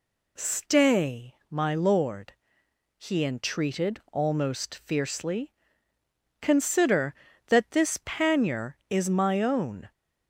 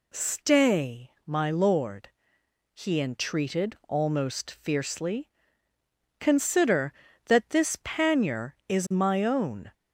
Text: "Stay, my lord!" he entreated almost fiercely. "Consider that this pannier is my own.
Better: neither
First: none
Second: none

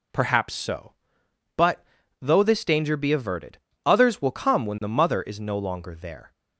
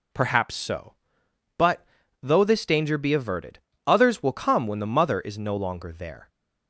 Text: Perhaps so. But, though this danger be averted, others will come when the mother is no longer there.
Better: neither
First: none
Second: none

